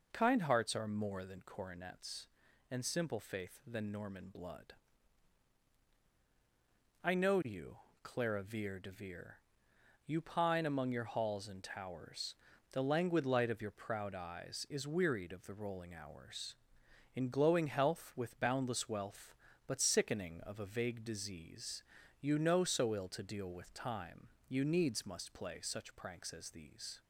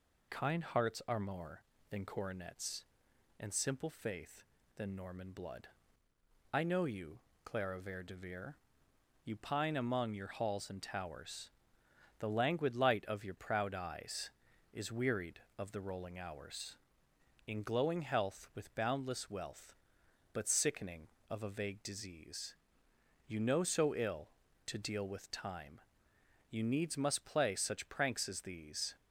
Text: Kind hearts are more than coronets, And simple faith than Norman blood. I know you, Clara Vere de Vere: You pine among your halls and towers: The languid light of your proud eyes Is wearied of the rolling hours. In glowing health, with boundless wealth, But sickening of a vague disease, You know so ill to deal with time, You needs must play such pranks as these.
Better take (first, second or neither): first